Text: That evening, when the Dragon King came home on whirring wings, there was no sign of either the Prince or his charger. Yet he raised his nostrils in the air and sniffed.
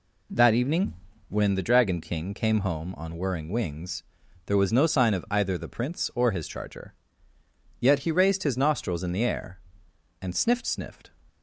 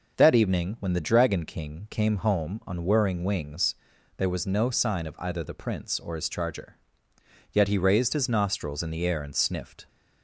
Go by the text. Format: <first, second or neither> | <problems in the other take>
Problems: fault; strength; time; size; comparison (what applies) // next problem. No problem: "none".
second | says "sniffed" twice; at 10.6 s